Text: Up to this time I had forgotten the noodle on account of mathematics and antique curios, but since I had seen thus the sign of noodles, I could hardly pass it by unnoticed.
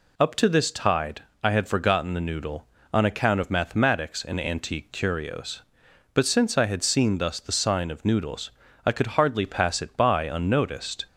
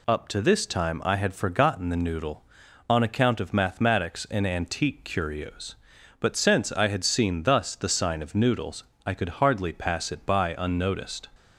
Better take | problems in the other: second | says "tide" for "time"; at 0.7 s

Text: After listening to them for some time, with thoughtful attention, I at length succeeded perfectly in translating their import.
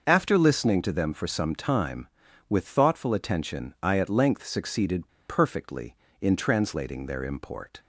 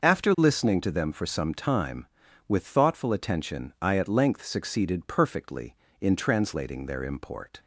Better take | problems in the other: second | starts louder than the rest; noticeable; until 1.0 s; 6 dB // pauses between "succeeded" and "perfectly"; slight; at 5.0 s; 0.20 s long

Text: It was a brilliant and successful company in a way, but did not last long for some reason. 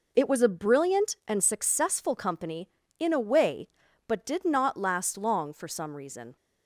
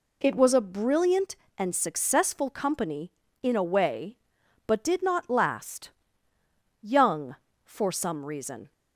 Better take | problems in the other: first | says "young" for "long"; at 6.7 s

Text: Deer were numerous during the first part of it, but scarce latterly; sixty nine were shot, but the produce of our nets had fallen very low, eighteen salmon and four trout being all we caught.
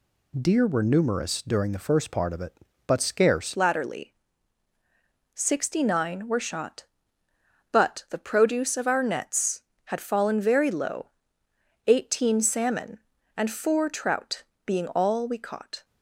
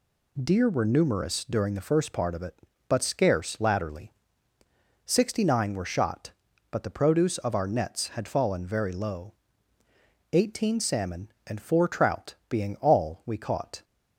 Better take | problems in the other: second | changes voice at "latterly"; from 3.5 s on; 12.3 s long // pauses between "trout" and "being"; slight; at 14.4 s; 0.22 s long

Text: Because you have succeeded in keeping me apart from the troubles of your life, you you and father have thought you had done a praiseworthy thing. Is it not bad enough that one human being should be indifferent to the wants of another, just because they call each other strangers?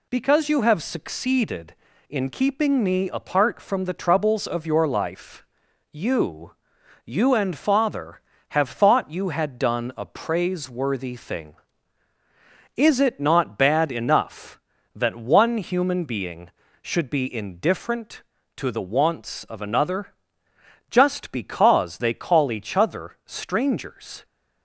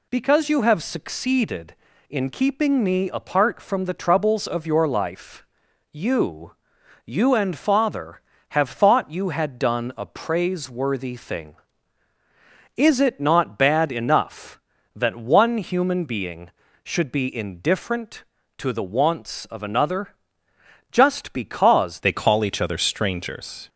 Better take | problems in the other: first | pauses between "you" and "you"; noticeable; at 6.5 s; 0.52 s long; noticeable in the first // changes voice at "they"; from 22.0 s on; 1.6 s long

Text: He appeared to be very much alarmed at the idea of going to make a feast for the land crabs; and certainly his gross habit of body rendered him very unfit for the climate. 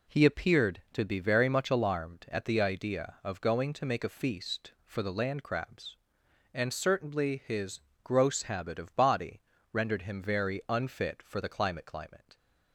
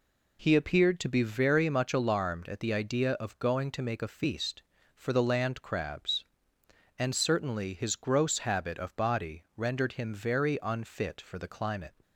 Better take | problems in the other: second | pauses between "his" and "gross"; slight; at 7.8 s; 0.22 s long // pauses between "body" and "rendered"; slight; at 9.4 s; 0.28 s long // says "climate" twice; at 11.8 s

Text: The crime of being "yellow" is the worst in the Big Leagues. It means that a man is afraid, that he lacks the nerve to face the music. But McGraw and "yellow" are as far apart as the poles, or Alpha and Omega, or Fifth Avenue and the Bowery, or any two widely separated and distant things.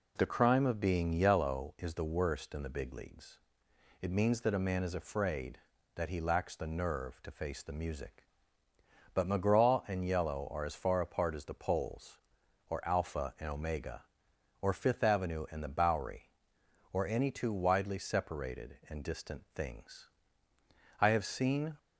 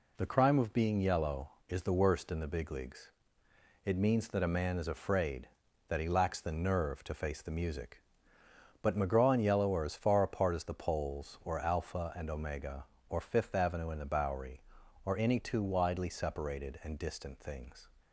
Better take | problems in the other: second | goes on to say "I have seen"; noticeable; from 20.9 s on; 0.78 s long

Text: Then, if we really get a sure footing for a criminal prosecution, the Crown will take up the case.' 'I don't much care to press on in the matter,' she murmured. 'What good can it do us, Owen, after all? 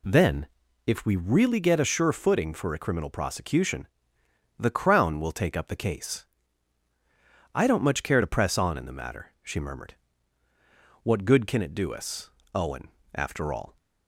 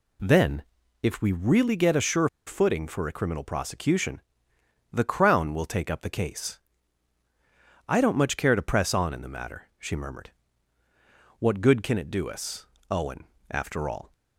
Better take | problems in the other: first | pauses between "sure" and "footing"; slight; at 2.2 s; 0.18 s long

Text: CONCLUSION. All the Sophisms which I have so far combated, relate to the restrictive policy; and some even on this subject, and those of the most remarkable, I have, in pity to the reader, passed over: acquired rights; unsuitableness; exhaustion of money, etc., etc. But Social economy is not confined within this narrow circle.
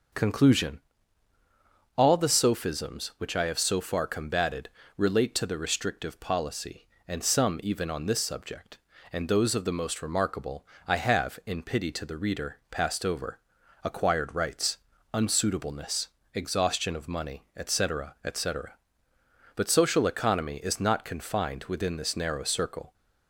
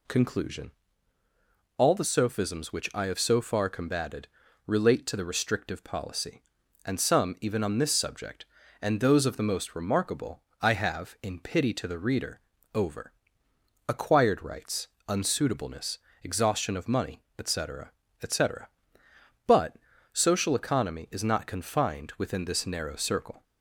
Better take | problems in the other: first | skips "passed"; at 12.5 s // pauses between "But" and "Social"; at 19.7 s; 0.38 s long

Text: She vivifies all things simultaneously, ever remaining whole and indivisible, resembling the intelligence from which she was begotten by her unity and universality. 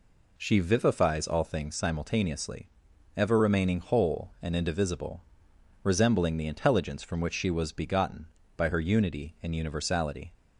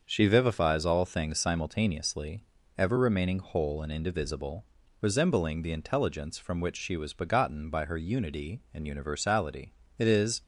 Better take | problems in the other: first | starts louder than the rest; until 1.0 s; 6.5 dB // goes on to say "It is"; slight; from 9.9 s on; 0.44 s long

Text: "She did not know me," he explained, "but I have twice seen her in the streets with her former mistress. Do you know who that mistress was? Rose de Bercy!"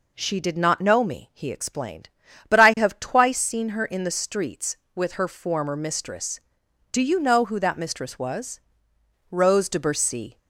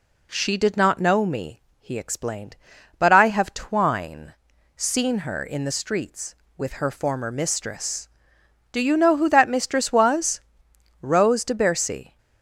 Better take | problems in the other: first | says "twine" for "twice"; at 3.5 s

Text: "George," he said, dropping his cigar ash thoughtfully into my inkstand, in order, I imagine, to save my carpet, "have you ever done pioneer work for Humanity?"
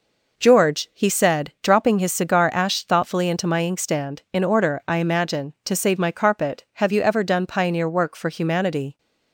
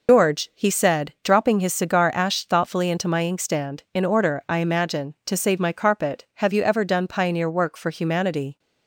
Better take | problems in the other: first | loses the start of "George"; at 0.0 s; 105 ms

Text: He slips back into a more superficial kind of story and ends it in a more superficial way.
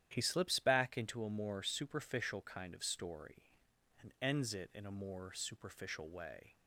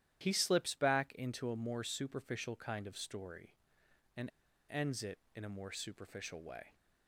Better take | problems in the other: first | starts louder than the rest; strong; until 1.2 s; 11.5 dB; strong in the first // pauses between "and" and "ends"; at 4.2 s; 0.40 s long

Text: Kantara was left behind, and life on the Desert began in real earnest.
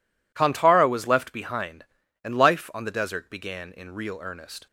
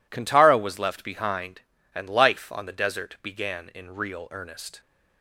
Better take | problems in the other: neither | none

